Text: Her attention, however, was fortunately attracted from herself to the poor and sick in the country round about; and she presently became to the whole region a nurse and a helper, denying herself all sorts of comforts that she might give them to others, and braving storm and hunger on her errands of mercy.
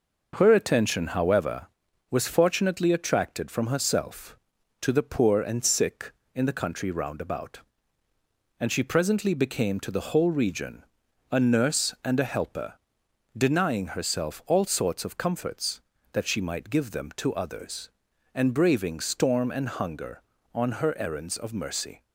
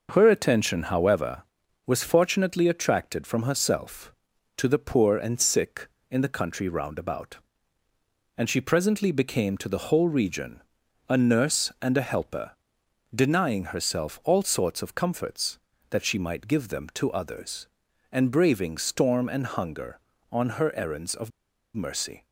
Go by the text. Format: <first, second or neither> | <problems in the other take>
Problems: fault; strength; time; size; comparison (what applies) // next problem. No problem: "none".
first | pauses between "region" and "a"; noticeable; at 10.6 s; 0.46 s long; noticeable in the first // pauses between "of" and "mercy"; at 21.2 s; 0.44 s long